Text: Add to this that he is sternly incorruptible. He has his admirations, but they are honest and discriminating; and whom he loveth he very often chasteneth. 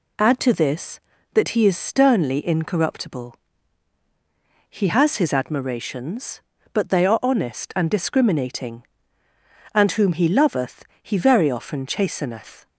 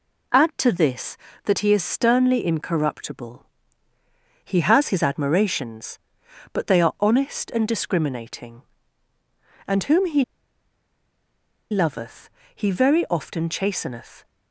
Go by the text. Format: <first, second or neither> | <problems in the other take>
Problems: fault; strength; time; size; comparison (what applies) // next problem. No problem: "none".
first | pauses between "he" and "loveth"; strong; at 10.2 s; 1.4 s long // pauses between "loveth" and "he"; slight; at 12.3 s; 0.24 s long; slight in the first